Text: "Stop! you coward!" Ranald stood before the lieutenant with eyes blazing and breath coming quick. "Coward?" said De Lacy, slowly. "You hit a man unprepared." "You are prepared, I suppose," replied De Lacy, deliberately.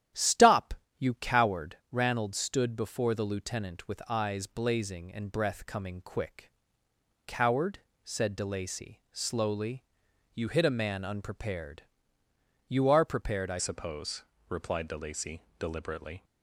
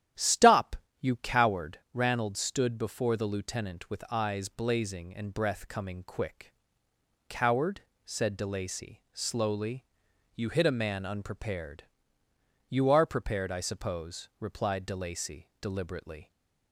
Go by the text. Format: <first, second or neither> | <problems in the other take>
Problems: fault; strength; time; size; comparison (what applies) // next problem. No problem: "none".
second | starts louder than the rest; strong; until 1.3 s; 11 dB; strong in the second // changes voice at "suppose"; from 13.5 s on; 2.7 s long